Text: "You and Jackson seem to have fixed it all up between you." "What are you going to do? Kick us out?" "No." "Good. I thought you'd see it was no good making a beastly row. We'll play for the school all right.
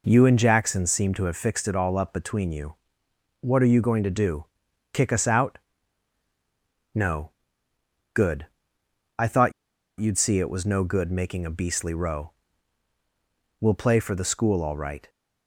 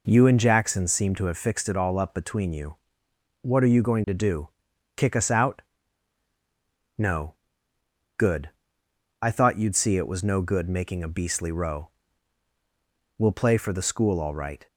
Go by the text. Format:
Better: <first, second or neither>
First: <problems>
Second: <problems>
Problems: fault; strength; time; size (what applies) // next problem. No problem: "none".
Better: second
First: pauses between "thought" and "you'd"; noticeable; at 9.5 s; 0.48 s long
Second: none